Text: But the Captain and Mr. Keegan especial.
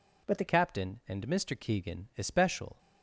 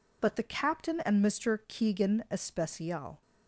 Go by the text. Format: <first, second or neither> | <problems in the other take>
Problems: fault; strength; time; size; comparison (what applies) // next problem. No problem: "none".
second | changes voice at "Captain"; from 0.4 s on; 2.3 s long